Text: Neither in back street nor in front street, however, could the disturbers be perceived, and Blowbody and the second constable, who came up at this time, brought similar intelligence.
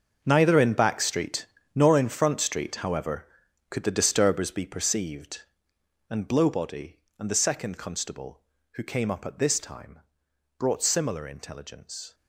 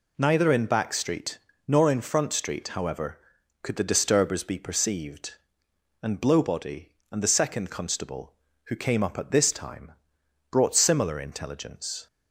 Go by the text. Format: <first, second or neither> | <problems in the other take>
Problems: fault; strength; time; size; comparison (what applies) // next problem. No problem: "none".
second | gets quieter; strong; throughout; 14 dB // pauses between "street" and "nor"; slight; at 1.4 s; 0.28 s long; slight in the second